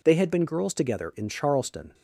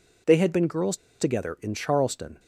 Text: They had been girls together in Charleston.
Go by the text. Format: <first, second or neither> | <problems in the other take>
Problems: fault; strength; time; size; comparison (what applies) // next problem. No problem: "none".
first | pauses between "girls" and "together"; slight; at 0.9 s; 0.23 s long